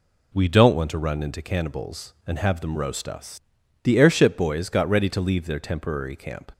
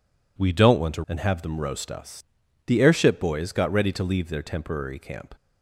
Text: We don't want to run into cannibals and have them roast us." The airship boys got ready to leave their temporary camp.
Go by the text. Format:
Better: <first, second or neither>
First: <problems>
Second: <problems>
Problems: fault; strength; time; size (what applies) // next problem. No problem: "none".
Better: first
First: none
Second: skips "run into cannibals"; at 1.0 s